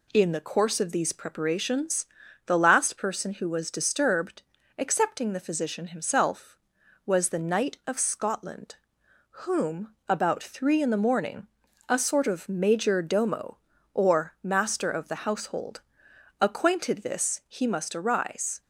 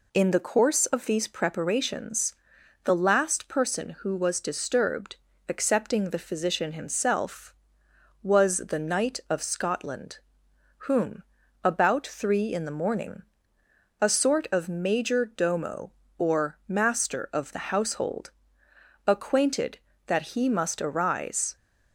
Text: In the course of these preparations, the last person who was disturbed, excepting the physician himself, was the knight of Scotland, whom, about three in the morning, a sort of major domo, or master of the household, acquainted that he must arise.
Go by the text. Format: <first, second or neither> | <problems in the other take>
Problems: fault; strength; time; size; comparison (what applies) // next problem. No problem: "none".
second | says "this" for "that"; at 17.0 s